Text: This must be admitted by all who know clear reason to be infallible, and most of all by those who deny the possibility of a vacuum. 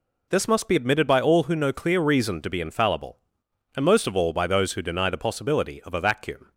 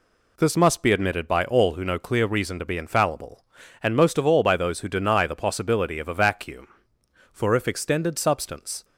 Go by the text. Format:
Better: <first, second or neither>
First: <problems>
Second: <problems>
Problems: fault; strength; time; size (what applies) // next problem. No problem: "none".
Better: first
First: none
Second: goes on to say "For if extended substance"; from 7.3 s on; 1.5 s long